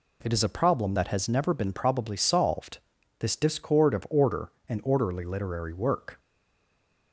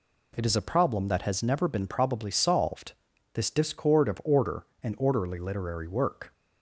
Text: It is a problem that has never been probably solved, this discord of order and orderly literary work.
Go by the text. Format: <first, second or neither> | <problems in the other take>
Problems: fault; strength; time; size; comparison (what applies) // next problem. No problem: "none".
second | stays silent after the last word; slight; from 6.1 s on; 1.0 s long